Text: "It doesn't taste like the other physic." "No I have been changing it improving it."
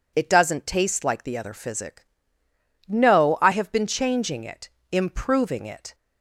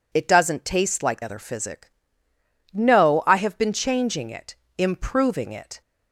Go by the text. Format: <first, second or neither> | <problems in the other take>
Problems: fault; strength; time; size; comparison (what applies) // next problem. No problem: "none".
first | skips "the"; at 1.2 s // pauses between "it" and "improving"; slight; at 4.5 s; 0.22 s long; slight in the first